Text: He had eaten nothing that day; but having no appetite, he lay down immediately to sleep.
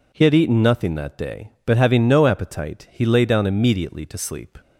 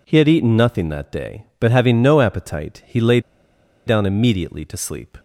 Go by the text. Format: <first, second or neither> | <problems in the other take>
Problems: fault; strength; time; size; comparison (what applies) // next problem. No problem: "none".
first | pauses between "lay" and "down"; noticeable; at 3.1 s; 0.67 s long